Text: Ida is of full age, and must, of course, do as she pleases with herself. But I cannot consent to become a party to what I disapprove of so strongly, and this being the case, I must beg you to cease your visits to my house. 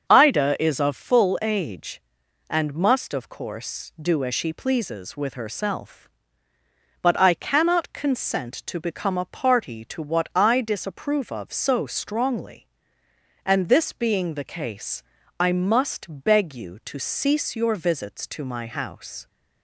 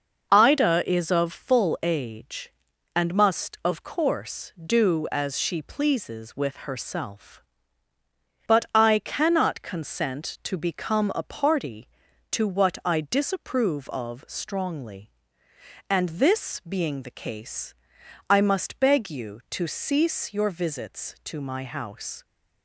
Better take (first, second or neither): first